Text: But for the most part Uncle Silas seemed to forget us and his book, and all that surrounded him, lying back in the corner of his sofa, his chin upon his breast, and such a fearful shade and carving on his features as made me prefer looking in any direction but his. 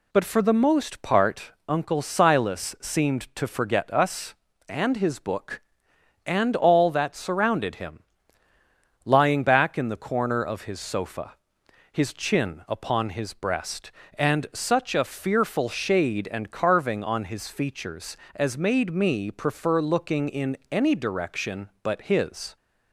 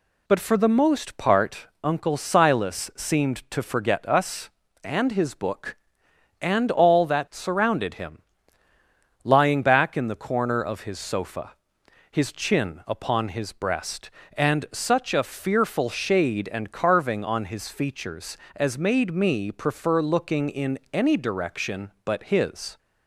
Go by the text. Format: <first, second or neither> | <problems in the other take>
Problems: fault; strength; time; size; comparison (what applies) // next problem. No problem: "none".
neither | pauses between "part" and "Uncle"; slight; the same in both // pauses between "in" and "any"; slight; the same in both